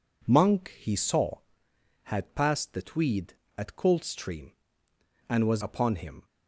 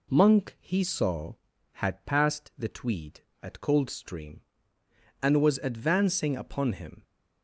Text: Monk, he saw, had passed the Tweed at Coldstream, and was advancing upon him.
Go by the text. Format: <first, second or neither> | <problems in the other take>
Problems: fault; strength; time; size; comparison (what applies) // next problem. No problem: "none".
second | skips "advancing"; at 5.6 s